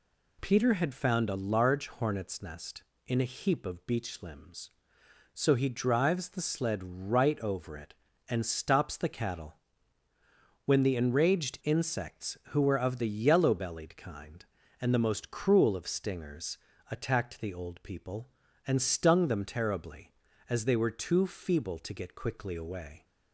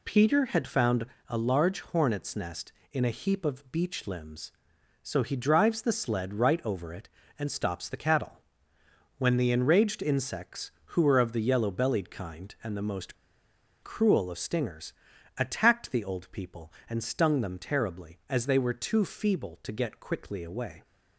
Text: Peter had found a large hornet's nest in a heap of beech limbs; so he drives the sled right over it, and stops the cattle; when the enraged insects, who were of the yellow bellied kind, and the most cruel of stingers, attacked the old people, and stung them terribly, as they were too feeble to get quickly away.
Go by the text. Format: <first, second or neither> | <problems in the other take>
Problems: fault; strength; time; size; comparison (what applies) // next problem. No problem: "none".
first | pauses between "found" and "a"; slight; at 1.0 s; 0.22 s long // pauses between "most" and "cruel"; noticeable; at 13.1 s; 0.68 s long